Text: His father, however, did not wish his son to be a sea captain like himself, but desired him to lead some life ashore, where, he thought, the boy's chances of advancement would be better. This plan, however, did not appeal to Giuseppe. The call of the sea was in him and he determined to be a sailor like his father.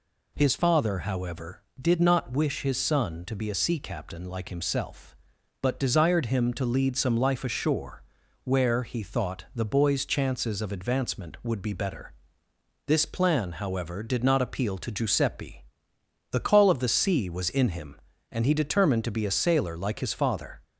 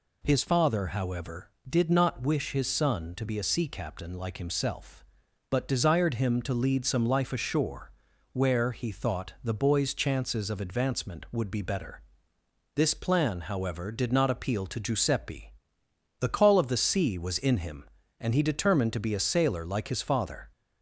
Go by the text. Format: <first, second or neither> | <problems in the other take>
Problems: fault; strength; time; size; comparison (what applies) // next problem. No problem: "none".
neither | none